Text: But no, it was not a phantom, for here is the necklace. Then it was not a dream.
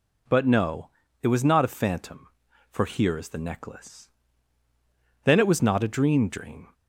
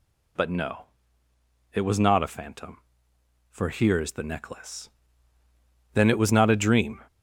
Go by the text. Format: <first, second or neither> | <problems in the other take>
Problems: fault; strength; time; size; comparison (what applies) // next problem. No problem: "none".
second | says "dream" twice; at 6.2 s